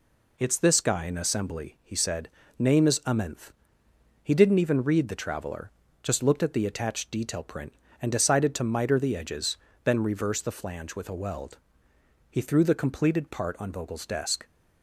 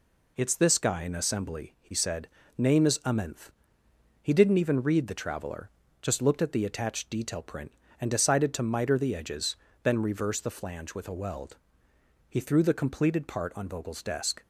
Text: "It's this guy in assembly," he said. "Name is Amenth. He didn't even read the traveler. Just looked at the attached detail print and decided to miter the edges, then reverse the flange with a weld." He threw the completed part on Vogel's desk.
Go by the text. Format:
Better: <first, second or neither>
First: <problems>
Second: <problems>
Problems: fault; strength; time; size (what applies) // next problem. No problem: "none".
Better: neither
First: none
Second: none